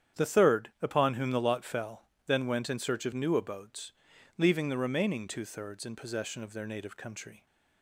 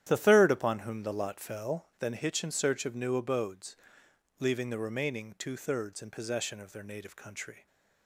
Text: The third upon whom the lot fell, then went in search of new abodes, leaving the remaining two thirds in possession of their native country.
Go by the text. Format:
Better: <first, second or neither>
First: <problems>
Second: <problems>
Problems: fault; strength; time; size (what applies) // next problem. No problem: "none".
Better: first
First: starts louder than the rest; strong; until 1.2 s; 9 dB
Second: starts louder than the rest; strong; until 1.0 s; 11 dB // says "hitch" for "went"; at 2.1 s